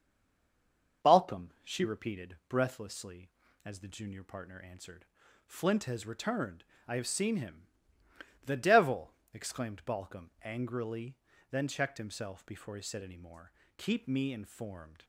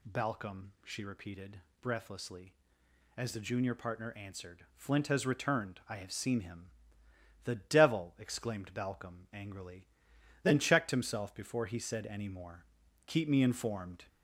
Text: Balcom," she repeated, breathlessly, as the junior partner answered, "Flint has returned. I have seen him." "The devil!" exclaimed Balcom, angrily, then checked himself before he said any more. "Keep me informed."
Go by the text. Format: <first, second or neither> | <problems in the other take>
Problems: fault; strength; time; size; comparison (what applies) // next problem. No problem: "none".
second | stays silent before the first word; until 1.0 s; 1.0 s long // starts louder than the rest; until 2.1 s; 6 dB